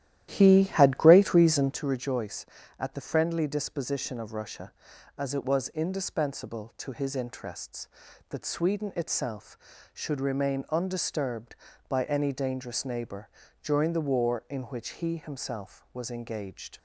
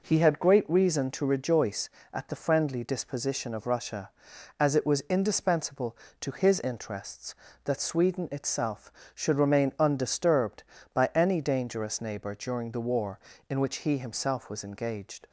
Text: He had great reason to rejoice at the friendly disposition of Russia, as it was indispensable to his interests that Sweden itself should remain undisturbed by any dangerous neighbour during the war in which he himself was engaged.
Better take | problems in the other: second | starts louder than the rest; strong; until 1.8 s; 12.5 dB // pauses between "neighbour" and "during"; slight; at 13.2 s; 0.36 s long

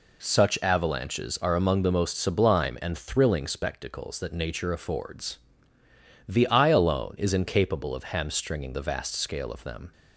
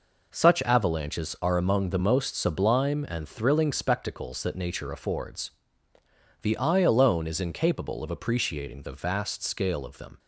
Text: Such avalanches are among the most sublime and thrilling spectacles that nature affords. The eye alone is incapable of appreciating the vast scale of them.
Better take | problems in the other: second | says "hamstringing" for "appreciating"; at 8.0 s

